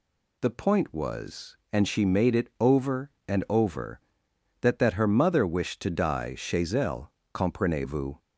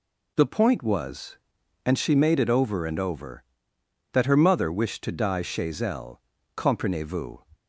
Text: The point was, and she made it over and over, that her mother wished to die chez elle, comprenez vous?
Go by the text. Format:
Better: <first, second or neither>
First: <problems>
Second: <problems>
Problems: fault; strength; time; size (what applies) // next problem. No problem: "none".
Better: second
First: says "that" twice; at 4.7 s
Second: none